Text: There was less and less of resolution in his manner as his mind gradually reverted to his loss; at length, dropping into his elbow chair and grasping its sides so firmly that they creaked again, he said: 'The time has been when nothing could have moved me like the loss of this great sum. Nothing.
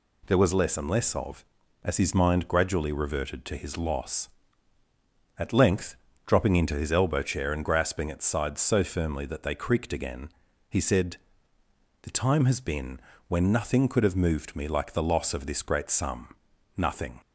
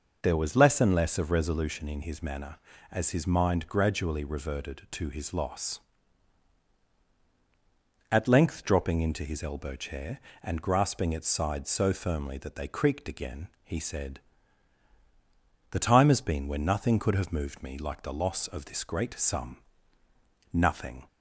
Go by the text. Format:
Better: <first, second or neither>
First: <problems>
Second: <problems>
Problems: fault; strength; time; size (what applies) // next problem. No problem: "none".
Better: second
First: skips "resolution in his manner"; at 1.6 s // pauses between "been" and "when"; slight; at 13.0 s; 0.28 s long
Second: none